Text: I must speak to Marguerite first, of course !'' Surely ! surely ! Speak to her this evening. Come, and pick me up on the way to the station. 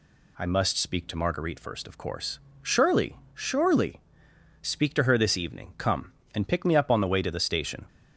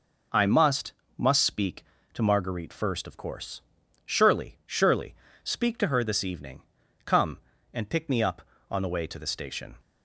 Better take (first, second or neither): first